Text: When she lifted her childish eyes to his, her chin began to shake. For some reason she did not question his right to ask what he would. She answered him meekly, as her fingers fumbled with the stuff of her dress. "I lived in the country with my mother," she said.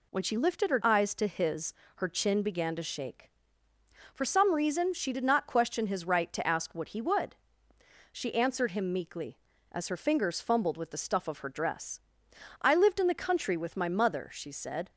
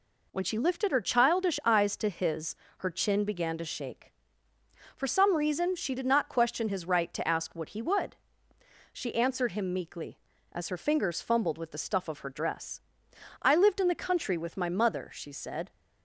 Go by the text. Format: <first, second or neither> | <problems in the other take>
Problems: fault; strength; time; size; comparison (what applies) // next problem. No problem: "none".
second | skips "childish"; at 0.8 s